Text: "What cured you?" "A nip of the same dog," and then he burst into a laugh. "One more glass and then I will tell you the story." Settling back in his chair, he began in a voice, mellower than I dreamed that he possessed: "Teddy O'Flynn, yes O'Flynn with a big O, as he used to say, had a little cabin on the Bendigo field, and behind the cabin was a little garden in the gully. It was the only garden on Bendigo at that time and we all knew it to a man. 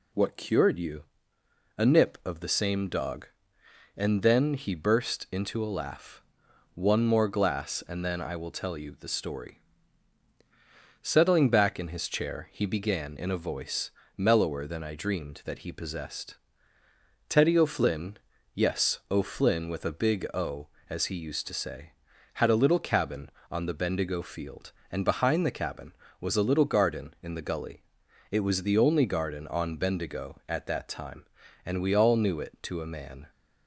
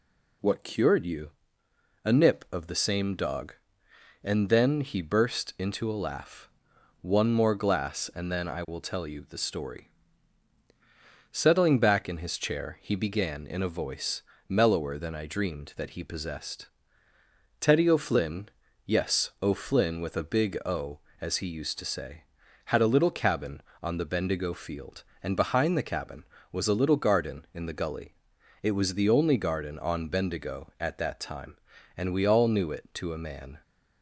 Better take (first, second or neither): neither